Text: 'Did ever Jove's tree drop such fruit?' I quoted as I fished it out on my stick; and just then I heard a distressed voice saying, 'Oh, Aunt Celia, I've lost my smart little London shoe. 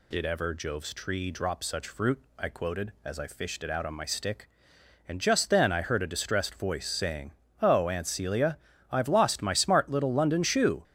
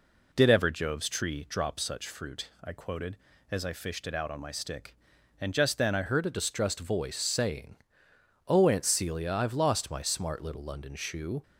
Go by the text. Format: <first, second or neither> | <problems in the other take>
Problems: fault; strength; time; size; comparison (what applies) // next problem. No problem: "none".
first | changes voice at "heard"; from 6.0 s on; 5.4 s long